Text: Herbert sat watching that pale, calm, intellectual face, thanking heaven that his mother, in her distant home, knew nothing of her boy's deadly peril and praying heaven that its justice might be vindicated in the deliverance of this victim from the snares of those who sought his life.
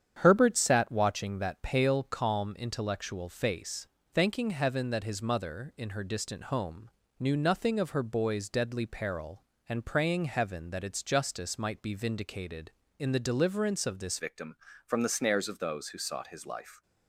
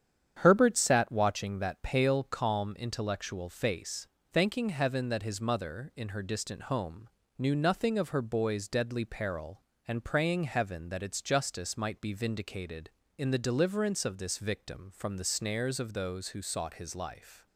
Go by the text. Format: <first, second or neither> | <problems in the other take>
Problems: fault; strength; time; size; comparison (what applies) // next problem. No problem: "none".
second | starts louder than the rest; strong; until 1.2 s; 8.5 dB; strong in the second // changes voice at "victim"; from 14.1 s on; 2.7 s long